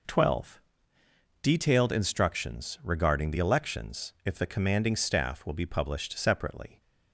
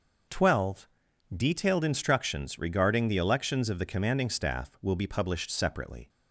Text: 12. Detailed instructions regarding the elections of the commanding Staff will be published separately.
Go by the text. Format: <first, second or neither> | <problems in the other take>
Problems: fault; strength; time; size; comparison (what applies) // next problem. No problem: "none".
second | says "if" for "of"; at 4.2 s